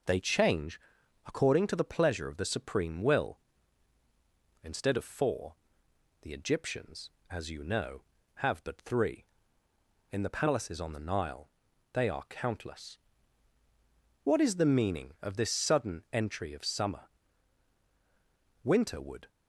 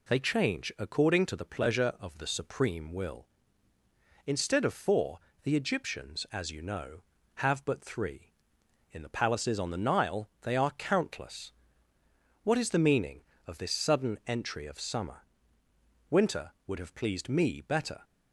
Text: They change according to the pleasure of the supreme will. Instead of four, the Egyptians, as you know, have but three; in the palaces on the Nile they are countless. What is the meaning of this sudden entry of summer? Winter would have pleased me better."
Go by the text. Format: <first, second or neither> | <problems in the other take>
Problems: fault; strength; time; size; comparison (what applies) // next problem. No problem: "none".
second | pauses between "change" and "according"; noticeable; at 0.7 s; 0.46 s long // pauses between "Nile" and "they"; at 11.4 s; 0.44 s long // stops before "have pleased me better"; at 19.2 s